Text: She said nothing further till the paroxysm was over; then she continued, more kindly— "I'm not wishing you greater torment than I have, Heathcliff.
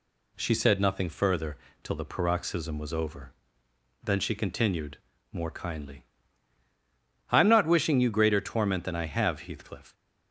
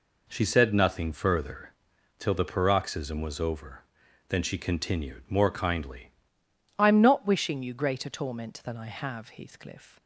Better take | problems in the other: first | pauses between "further" and "till"; noticeable; at 1.6 s; 0.50 s long; slight in the first // changes voice at "I'm"; from 6.7 s on; 3.3 s long

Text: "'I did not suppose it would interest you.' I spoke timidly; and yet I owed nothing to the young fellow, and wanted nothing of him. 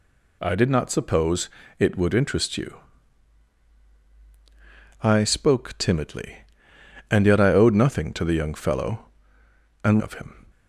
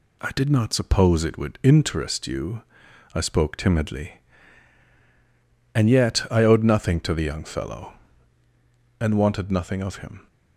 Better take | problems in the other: second | pauses between "suppose" and "it"; slight; at 1.4 s; 0.30 s long // skips "wanted nothing"; at 10.0 s

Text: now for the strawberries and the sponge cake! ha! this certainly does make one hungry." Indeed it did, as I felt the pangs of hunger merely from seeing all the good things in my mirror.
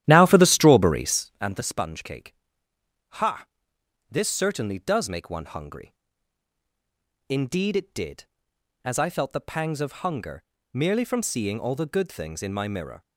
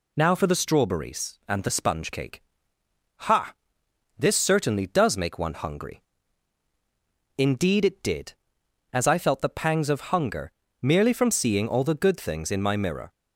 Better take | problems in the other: second | starts louder than the rest; strong; until 1.5 s; 12.5 dB // pauses between "hunger" and "merely"; slight; at 10.4 s; 0.32 s long; slight in the second

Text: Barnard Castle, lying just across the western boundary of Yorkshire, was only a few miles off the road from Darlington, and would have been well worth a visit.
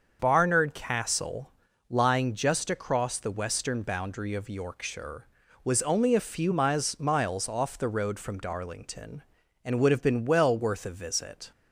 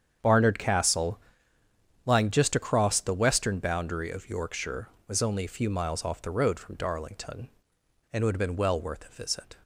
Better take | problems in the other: second | starts louder than the rest; until 1.2 s; 6.5 dB; strong in the second // says "miles" twice; at 6.9 s

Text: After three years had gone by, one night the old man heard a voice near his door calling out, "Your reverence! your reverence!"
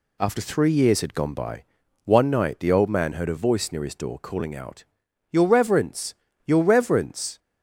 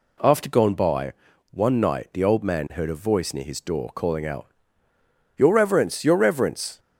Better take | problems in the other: first | skips "three years had"; at 0.4 s

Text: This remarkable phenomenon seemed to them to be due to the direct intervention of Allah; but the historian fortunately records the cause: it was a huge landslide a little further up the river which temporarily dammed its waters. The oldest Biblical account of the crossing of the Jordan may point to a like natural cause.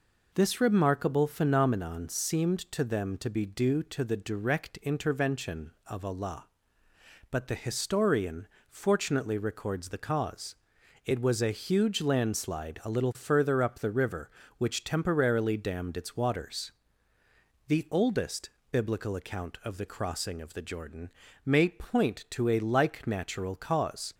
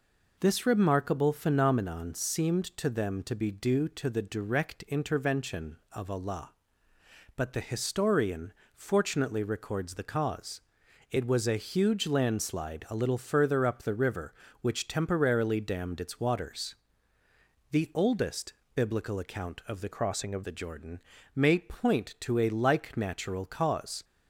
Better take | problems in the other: first | pauses between "historian" and "fortunately"; slight; at 8.5 s; 0.22 s long; slight in the first // pauses between "oldest" and "Biblical"; slight; at 18.5 s; 0.22 s long; slight in the first // changes voice from "crossing" to "of"; from 19.9 to 20.4 s; 0.5 s long // pauses between "Jordan" and "may"; slight; at 21.0 s; 0.34 s long; slight in the first

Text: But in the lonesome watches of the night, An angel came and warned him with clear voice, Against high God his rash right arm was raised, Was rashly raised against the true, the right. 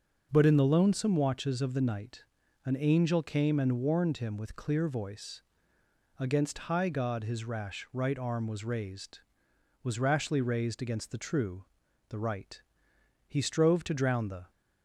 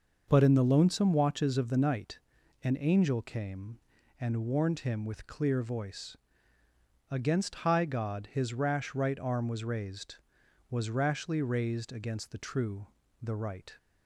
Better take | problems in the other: second | starts louder than the rest; until 1.3 s; 6 dB; also in the second // goes on to say "He strove to drown the"; noticeable; from 13.2 s on; 1.2 s long

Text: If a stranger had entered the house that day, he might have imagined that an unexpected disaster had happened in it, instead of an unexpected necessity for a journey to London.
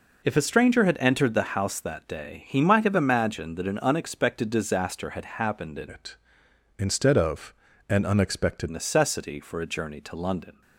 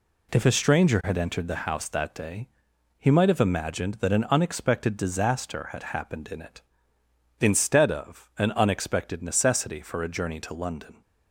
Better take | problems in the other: second | changes voice from "it" to "unexpected"; from 5.8 to 8.6 s; 2.8 s long // pauses between "of" and "an"; at 7.5 s; 0.38 s long

